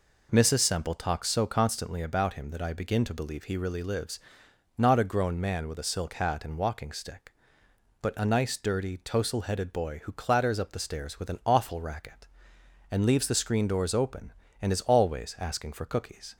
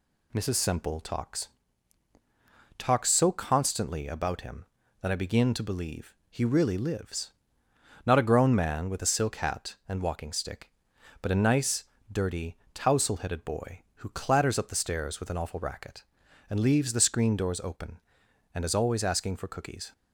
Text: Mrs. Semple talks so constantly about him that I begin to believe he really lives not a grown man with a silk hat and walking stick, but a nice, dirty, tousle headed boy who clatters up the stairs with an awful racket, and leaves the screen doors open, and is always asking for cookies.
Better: first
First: pauses between "lives" and "not"; noticeable; at 4.1 s; 0.58 s long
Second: says "talks" twice; at 2.7 s // pauses between "believe" and "he"; slight; at 6.1 s; 0.16 s long // pauses between "lives" and "not"; noticeable; at 7.3 s; 0.72 s long

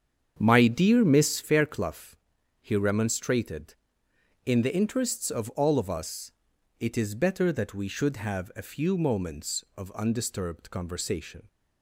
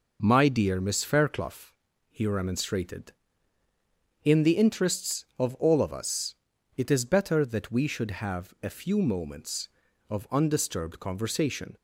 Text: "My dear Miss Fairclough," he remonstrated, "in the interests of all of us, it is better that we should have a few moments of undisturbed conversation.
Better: second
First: starts louder than the rest; strong; until 1.5 s; 8 dB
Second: none

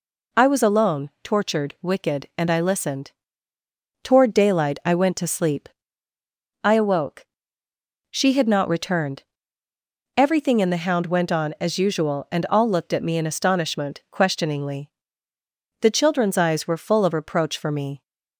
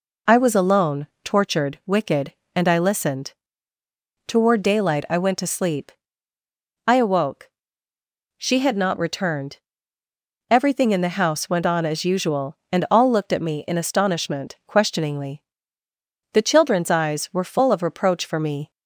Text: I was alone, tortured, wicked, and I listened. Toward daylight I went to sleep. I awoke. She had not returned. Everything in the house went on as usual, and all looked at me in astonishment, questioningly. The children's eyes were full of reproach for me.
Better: second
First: says "hound" for "house"; at 10.7 s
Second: none

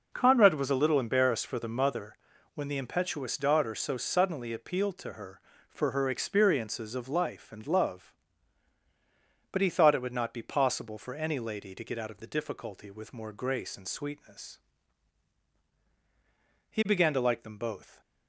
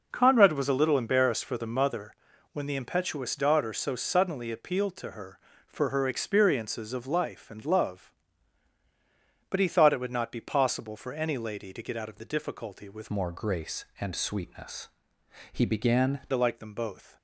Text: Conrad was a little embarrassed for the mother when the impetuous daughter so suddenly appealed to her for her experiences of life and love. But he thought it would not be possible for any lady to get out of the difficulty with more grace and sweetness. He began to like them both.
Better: first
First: pauses between "mother" and "when"; at 2.1 s; 0.38 s long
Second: pauses between "mother" and "when"; at 2.1 s; 0.38 s long // changes voice from "more" to "began"; from 13.0 to 16.1 s; 3.1 s long

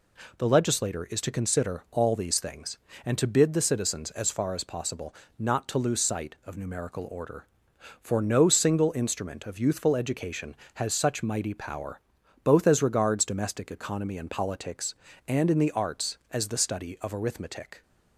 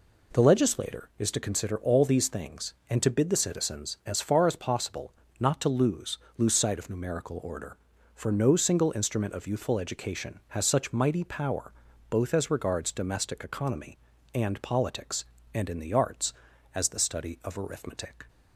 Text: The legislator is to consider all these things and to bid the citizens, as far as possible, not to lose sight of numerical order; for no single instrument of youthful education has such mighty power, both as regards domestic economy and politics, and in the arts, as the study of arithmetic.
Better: first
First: none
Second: says "lose" twice; at 6.3 s

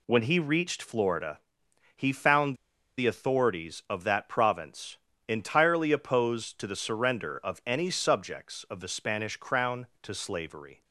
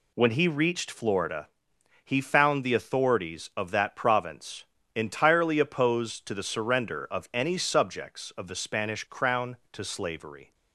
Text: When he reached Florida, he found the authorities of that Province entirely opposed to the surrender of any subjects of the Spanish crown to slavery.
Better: second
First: pauses between "found" and "the"; at 2.5 s; 0.41 s long // pauses between "Province" and "entirely"; slight; at 4.9 s; 0.28 s long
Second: pauses between "Province" and "entirely"; slight; at 4.6 s; 0.28 s long

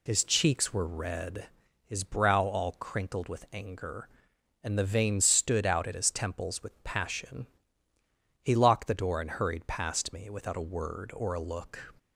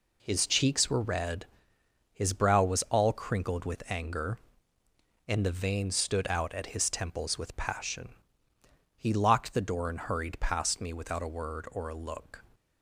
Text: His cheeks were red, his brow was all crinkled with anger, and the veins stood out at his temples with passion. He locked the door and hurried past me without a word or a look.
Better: second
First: skips "was"; at 2.4 s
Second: none

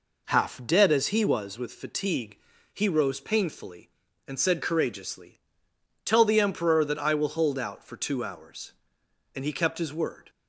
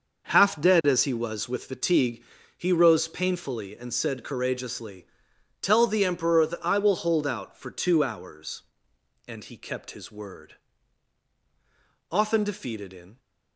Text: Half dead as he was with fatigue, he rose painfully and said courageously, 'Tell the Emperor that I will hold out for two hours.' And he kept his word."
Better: first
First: none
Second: goes on to say "Often defeated in"; noticeable; from 12.1 s on; 1.0 s long

